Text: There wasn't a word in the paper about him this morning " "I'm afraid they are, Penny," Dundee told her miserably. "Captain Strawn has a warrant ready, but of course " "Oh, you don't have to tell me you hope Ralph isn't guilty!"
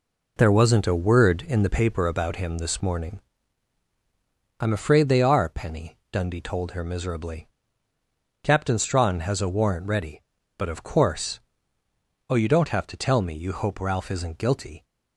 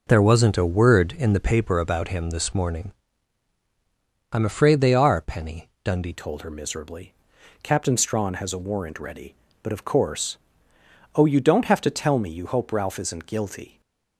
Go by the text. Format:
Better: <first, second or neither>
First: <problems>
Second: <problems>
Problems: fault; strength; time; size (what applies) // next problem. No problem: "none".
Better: first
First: none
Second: changes voice at "told"; from 6.1 s on; 7.7 s long // stays silent after the last word; slight; from 13.6 s on; 0.5 s long